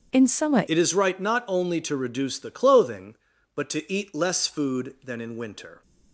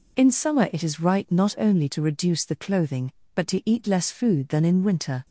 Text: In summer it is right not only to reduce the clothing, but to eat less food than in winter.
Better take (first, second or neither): second